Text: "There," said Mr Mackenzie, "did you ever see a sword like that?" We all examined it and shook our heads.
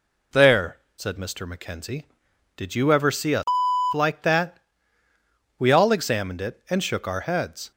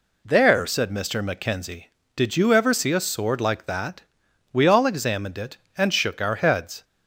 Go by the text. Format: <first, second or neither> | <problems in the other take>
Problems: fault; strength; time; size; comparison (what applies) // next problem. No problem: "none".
second | skips "sword"; at 3.6 s